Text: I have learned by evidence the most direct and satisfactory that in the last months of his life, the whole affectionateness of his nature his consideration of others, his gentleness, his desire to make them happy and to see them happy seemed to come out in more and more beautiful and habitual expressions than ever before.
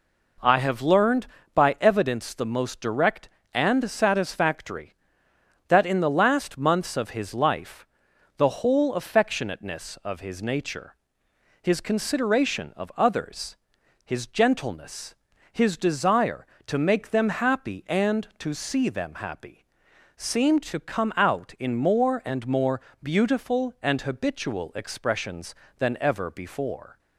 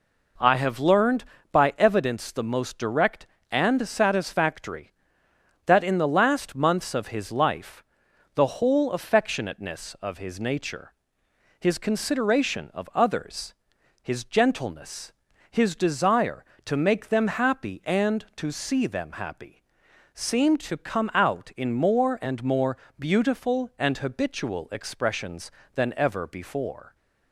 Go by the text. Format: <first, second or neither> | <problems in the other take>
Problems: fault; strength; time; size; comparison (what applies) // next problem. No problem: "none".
neither | pauses between "nature" and "his"; noticeable; the same in both // pauses between "happy" and "seemed"; noticeable; the same in both // pauses between "more" and "beautiful"; slight; the same in both